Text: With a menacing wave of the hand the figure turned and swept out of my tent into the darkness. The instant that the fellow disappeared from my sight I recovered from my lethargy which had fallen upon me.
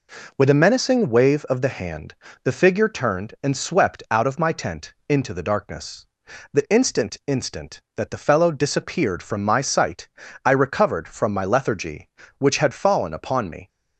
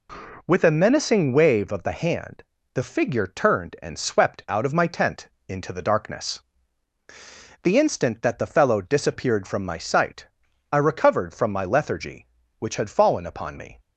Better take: second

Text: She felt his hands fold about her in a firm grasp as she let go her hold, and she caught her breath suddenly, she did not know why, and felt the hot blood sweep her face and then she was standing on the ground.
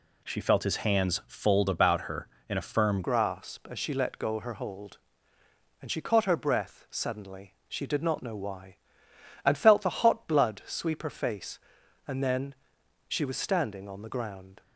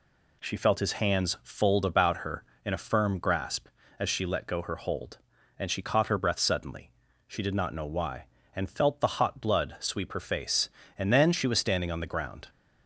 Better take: second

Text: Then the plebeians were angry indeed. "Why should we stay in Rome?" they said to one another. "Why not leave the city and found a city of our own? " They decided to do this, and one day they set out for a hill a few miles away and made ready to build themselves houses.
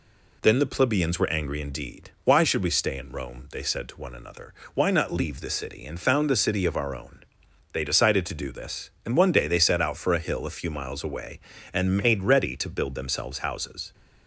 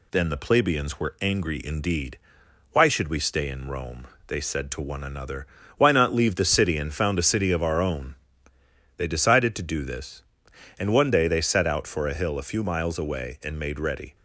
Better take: first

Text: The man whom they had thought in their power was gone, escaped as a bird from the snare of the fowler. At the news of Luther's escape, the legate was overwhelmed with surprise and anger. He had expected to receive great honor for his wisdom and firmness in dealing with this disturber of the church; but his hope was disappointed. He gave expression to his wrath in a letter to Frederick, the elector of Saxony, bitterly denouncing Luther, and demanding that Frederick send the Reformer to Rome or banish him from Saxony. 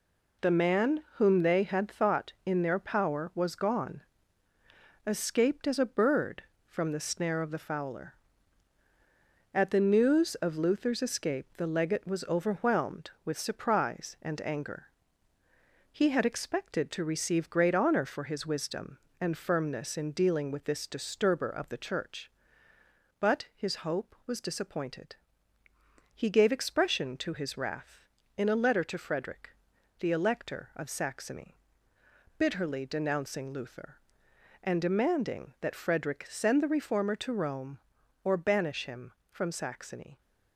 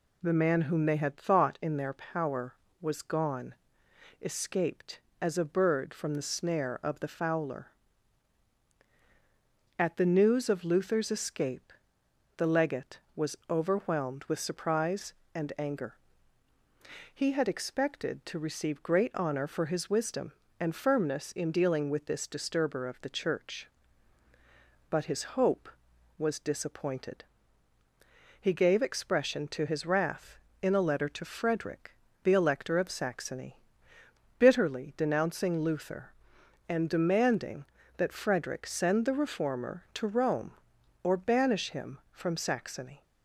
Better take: neither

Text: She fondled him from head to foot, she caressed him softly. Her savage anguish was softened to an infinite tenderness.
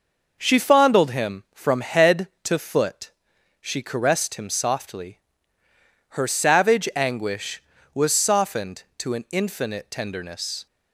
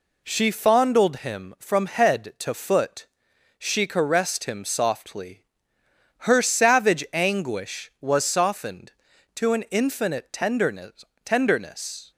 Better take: first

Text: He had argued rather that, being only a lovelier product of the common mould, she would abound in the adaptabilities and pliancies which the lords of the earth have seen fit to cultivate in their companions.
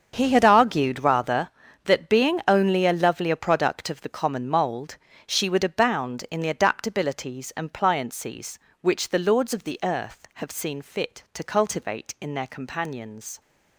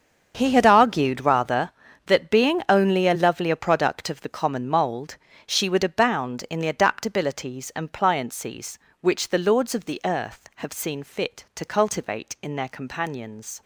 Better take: neither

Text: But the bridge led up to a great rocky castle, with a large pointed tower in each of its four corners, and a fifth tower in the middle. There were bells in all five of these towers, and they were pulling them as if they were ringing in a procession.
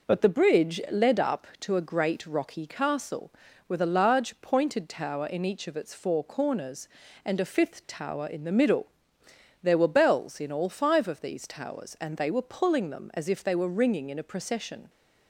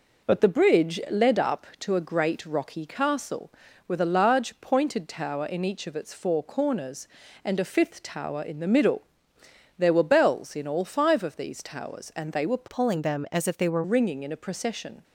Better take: first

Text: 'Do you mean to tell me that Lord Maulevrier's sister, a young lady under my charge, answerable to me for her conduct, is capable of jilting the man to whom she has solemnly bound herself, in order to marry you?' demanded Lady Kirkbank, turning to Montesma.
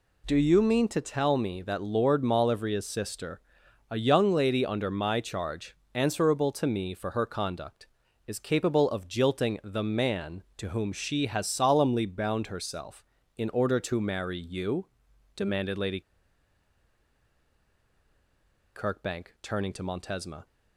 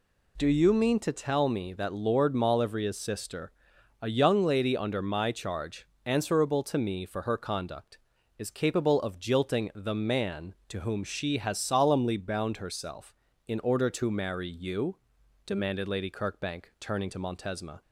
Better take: second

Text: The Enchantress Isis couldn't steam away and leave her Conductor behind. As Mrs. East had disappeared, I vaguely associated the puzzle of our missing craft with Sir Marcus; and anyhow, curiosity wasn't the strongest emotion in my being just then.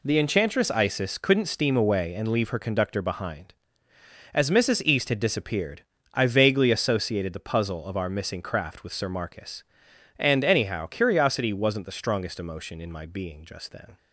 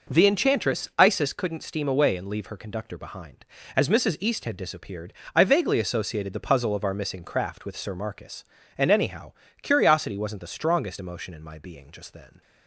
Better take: neither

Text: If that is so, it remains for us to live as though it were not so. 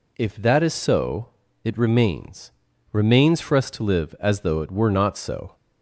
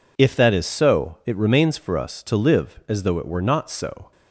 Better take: second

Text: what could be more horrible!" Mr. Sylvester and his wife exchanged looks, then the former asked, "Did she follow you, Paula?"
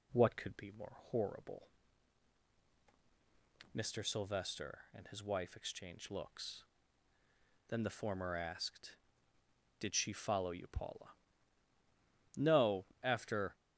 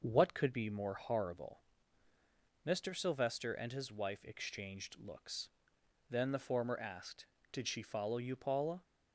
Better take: second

